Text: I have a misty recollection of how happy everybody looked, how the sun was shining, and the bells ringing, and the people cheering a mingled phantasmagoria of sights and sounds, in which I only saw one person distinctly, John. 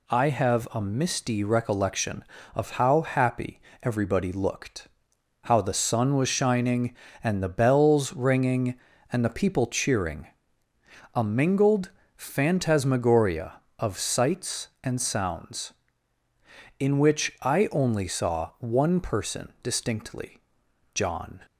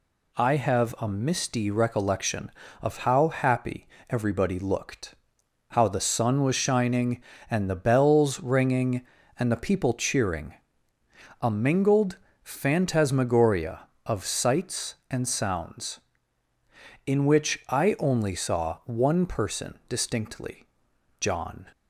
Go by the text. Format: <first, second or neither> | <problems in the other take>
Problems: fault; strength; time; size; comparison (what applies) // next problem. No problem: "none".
neither | pauses between "happy" and "everybody"; slight; the same in both // pauses between "cheering" and "a"; noticeable; the same in both // pauses between "mingled" and "phantasmagoria"; slight; the same in both